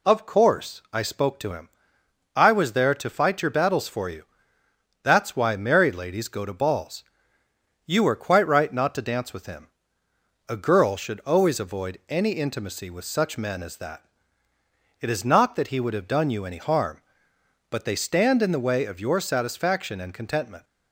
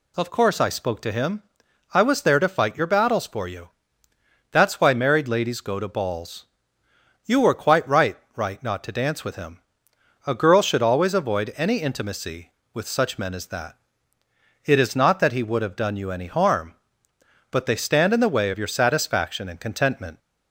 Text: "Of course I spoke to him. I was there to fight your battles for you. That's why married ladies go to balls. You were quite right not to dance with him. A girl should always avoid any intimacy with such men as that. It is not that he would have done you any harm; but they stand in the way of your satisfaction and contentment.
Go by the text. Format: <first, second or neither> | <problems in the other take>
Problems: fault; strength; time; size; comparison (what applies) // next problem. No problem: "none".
first | says "right" twice; at 8.3 s